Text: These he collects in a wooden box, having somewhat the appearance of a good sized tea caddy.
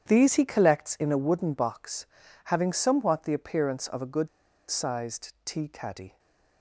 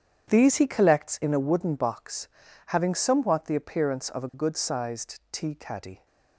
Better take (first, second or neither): second